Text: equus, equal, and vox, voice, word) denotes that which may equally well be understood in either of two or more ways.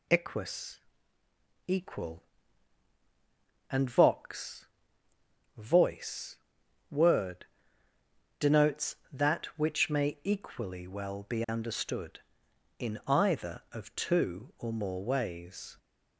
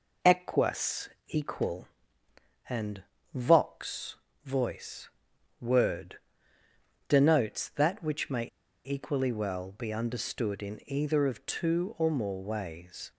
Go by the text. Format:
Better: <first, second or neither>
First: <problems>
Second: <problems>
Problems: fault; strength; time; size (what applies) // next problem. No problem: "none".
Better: first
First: none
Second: pauses between "and" and "vox"; slight; at 3.0 s; 0.32 s long // pauses between "may" and "equally"; at 8.4 s; 0.39 s long